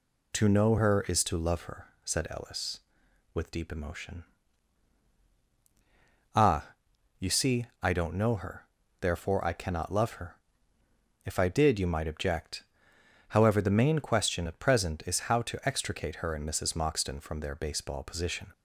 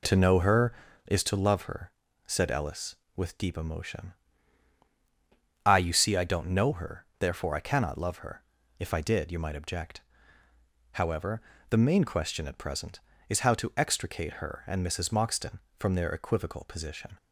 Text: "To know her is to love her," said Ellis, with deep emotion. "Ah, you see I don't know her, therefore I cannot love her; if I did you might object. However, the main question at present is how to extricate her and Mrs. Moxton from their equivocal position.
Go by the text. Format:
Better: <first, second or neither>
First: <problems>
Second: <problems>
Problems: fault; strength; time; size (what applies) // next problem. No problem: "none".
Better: second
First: pauses between "see" and "I"; slight; at 7.6 s; 0.16 s long // says "baseball" for "equivocal"; at 17.5 s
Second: none